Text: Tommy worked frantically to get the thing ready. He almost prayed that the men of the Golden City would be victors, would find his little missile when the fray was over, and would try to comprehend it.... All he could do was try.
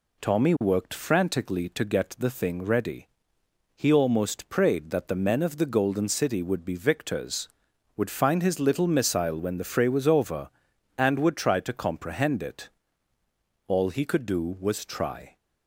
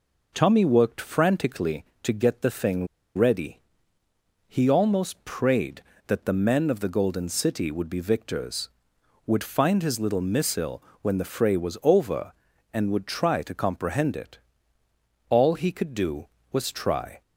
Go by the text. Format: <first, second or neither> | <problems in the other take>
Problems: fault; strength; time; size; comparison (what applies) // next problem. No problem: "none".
first | pauses between "thing" and "ready"; slight; at 2.8 s; 0.30 s long // pauses between "missile" and "when"; slight; at 10.8 s; 0.18 s long